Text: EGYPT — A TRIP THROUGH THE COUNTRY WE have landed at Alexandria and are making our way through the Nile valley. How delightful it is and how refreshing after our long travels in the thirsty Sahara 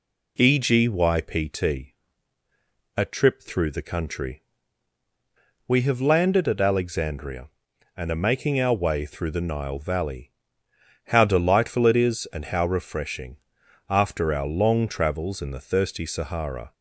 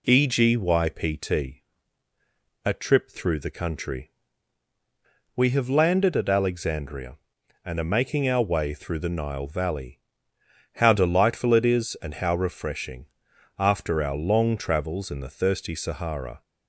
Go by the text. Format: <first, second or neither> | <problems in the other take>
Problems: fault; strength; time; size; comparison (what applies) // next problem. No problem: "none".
neither | pauses between "COUNTRY" and "WE"; the same in both // pauses between "refreshing" and "after"; noticeable; the same in both